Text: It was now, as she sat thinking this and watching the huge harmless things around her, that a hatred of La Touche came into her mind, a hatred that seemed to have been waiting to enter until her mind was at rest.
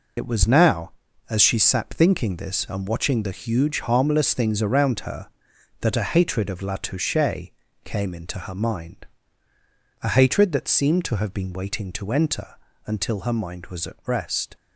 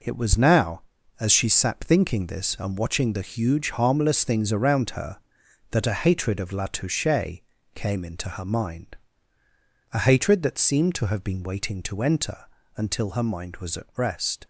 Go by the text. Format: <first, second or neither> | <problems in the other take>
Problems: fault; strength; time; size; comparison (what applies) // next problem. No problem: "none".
second | loses the start of "It"; at 0.1 s; 55 ms // pauses between "Touche" and "came"; slight; at 7.4 s; 0.34 s long; slight in the second // pauses between "enter" and "until"; slight; at 12.5 s; 0.30 s long; slight in the second